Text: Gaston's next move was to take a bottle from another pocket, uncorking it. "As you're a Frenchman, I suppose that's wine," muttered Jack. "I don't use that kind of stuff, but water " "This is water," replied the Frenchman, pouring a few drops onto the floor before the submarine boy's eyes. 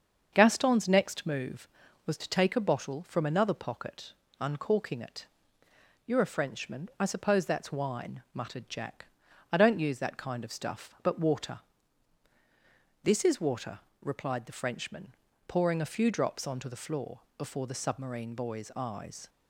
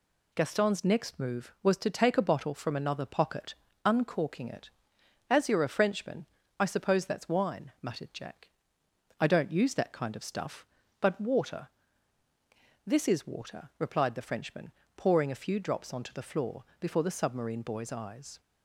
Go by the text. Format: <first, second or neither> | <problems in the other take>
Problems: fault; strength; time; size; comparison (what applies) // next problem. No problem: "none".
second | starts louder than the rest; until 1.3 s; 7 dB // skips "As"; at 5.6 s // pauses between "floor" and "before"; slight; at 17.2 s; 0.18 s long; slight in the second